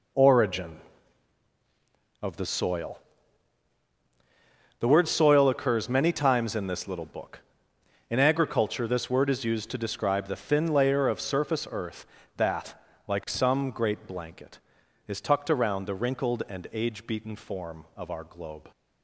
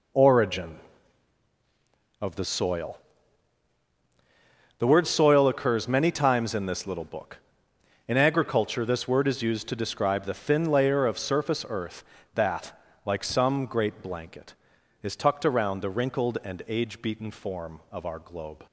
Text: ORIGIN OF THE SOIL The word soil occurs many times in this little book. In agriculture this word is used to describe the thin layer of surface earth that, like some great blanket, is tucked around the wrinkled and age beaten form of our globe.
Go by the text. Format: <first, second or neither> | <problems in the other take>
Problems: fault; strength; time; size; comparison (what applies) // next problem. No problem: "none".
neither | pauses between "SOIL" and "The"; strong; the same in both